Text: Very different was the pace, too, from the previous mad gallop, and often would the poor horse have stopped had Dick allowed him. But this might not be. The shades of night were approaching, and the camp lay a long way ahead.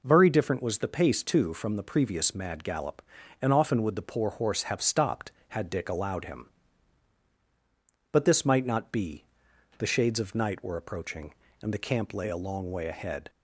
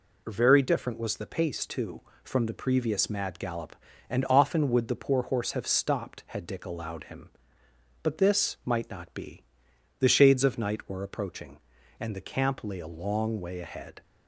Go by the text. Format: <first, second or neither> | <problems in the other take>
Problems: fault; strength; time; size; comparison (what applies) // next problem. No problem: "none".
neither | none